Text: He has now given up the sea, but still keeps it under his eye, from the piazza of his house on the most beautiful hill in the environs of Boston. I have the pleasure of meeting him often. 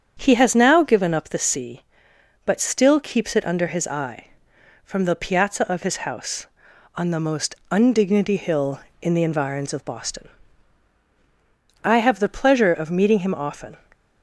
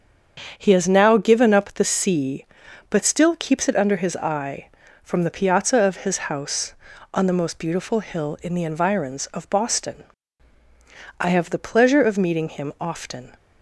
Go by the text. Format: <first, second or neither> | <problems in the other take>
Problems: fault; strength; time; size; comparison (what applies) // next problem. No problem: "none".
second | starts louder than the rest; strong; until 1.1 s; 8 dB; strong in the second // says "undignity" for "beautiful"; at 7.7 s